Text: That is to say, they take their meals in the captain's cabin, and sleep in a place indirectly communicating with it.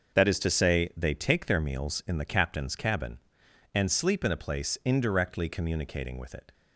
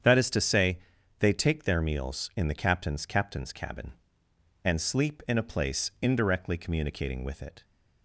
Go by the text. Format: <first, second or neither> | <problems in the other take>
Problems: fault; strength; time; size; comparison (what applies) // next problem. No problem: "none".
first | starts louder than the rest; strong; until 1.4 s; 8 dB; also in the first // says "captain's" twice; at 3.0 s